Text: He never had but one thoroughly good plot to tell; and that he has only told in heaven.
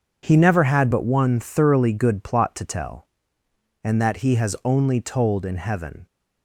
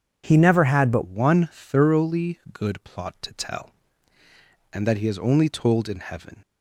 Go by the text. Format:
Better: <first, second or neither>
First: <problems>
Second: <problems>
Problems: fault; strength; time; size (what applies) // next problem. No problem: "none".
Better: first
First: none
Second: changes voice at "one"; from 1.0 s on; 5.4 s long